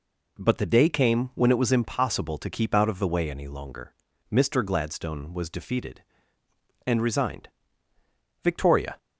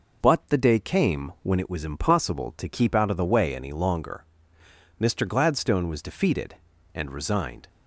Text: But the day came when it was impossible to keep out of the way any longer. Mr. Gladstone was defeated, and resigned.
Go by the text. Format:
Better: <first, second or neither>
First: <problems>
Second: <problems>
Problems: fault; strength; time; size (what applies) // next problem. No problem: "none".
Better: second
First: goes on to say "Victoria"; from 8.4 s on; 0.54 s long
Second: none